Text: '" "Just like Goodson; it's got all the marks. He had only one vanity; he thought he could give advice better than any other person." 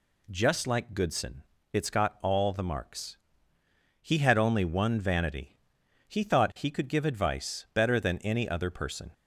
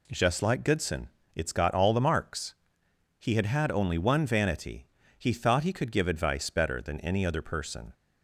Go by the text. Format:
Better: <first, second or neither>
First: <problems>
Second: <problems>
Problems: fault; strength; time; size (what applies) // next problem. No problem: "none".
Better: first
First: none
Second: says "had" twice; at 3.4 s